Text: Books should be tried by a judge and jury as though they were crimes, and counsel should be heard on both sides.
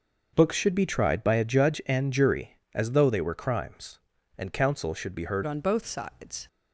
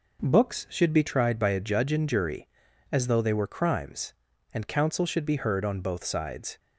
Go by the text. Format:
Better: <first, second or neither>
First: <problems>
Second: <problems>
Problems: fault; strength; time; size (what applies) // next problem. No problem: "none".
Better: second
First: starts louder than the rest; until 1.3 s; 6.5 dB // changes voice at "on"; from 5.4 s on; 1.0 s long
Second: none